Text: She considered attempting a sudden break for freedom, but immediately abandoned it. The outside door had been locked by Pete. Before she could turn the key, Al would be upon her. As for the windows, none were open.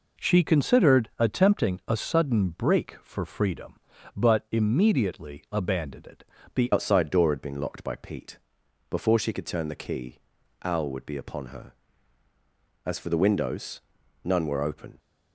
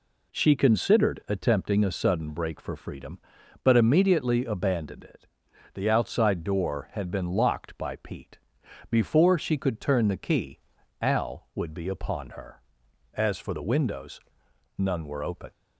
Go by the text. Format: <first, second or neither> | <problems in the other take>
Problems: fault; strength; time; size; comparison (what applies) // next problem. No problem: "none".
second | changes voice at "outside"; from 6.7 s on; 8.2 s long